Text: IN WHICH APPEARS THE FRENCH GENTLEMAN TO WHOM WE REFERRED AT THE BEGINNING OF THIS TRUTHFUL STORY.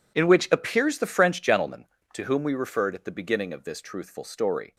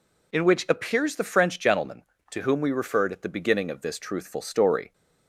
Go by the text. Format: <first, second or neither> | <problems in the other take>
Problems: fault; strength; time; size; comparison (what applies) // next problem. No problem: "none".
second | gets quieter; strong; throughout; 17 dB